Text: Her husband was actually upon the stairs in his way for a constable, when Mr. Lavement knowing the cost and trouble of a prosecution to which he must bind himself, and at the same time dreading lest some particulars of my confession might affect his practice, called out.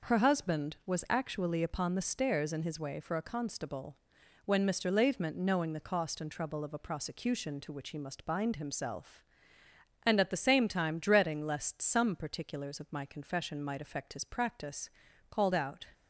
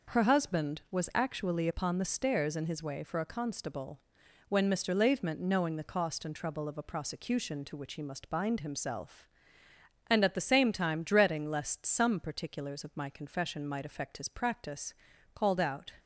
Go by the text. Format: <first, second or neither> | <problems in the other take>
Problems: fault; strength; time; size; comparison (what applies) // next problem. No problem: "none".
neither | none